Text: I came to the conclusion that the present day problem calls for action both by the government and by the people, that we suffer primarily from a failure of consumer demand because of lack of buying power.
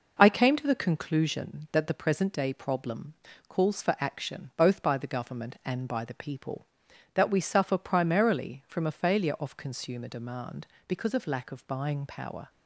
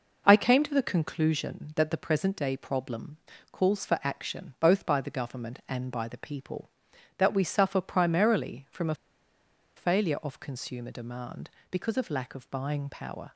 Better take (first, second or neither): first